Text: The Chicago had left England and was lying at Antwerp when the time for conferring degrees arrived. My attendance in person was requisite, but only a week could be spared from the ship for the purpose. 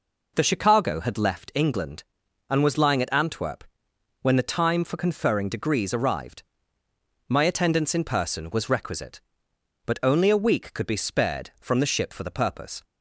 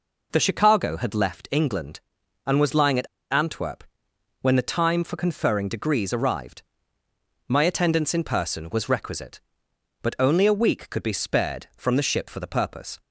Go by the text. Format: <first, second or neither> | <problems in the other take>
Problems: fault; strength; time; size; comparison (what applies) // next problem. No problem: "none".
first | pauses between "at" and "Antwerp"; slight; at 3.0 s; 0.24 s long // pauses between "Antwerp" and "when"; noticeable; at 3.8 s; 0.60 s long; noticeable in the first